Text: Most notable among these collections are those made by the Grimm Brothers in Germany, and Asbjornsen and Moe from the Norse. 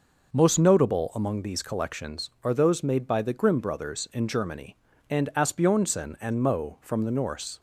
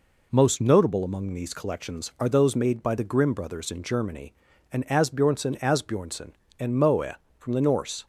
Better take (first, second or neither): first